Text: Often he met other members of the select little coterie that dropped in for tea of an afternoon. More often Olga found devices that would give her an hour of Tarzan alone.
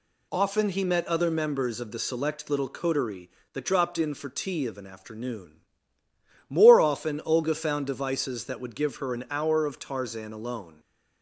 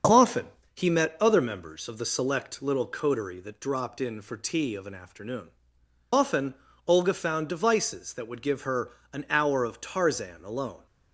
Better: first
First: none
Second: starts louder than the rest; until 1.4 s; 6.5 dB // pauses between "Often" and "he"; slight; at 0.4 s; 0.30 s long // skips "More"; at 5.8 s // pauses between "often" and "Olga"; slight; at 6.5 s; 0.30 s long // pauses between "her" and "an"; slight; at 8.8 s; 0.24 s long

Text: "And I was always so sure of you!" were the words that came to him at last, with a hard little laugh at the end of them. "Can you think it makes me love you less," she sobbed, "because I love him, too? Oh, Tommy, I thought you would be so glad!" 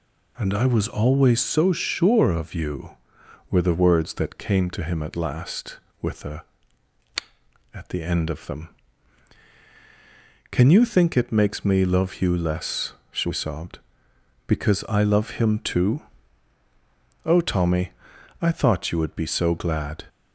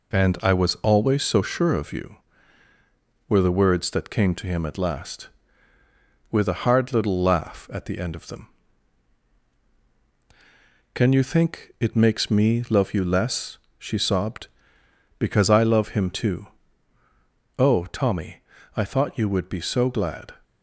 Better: second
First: skips "hard little laugh"; at 7.0 s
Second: none

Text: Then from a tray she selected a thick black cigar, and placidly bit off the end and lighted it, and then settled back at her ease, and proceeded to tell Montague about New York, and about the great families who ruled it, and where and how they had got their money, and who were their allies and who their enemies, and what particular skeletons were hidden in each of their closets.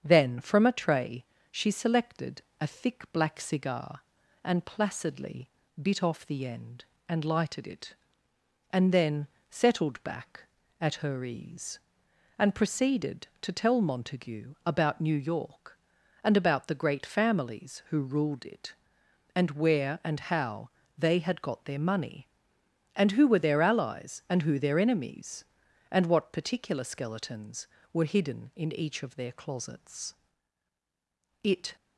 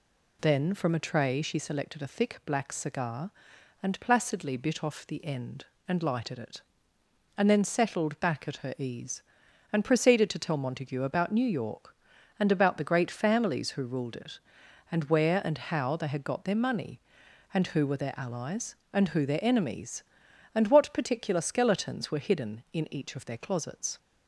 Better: second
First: starts louder than the rest; strong; until 1.0 s; 7.5 dB // pauses between "tray" and "she"; slight; at 1.2 s; 0.26 s long // pauses between "selected" and "a"; slight; at 2.4 s; 0.18 s long // pauses between "placidly" and "bit"; slight; at 5.5 s; 0.30 s long // pauses between "then" and "settled"; slight; at 9.2 s; 0.22 s long // pauses between "how" and "they"; slight; at 20.7 s; 0.26 s long // goes on to say "It"; slight; from 31.4 s on; 0.34 s long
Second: none

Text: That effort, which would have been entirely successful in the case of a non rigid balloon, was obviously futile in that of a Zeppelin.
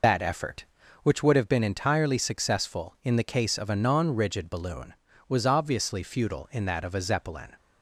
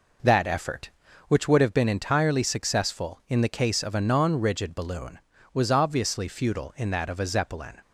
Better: second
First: loses the start of "That"; at 0.0 s; 90 ms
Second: none

